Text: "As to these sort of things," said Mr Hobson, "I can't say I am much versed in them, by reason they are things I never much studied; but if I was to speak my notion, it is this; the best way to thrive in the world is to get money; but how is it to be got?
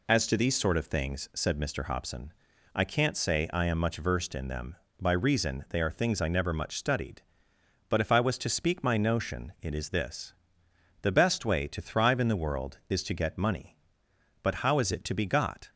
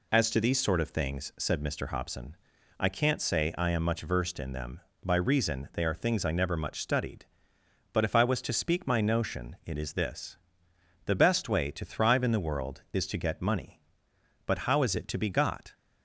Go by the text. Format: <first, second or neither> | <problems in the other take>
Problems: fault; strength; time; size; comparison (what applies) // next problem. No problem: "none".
neither | none